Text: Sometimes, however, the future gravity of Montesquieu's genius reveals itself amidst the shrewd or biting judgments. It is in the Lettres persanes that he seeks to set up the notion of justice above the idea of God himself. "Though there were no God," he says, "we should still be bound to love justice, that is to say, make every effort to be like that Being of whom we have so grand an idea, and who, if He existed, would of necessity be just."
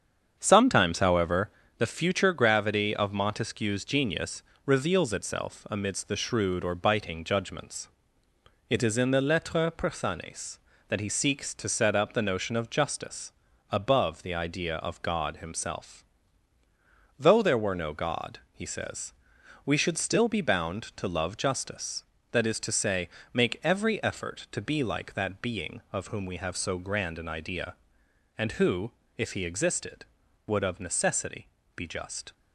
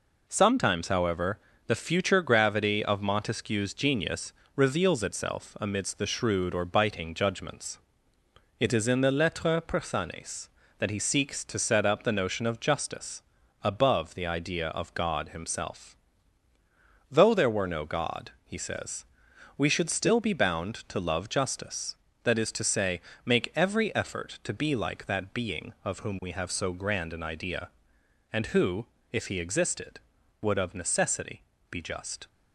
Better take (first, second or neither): second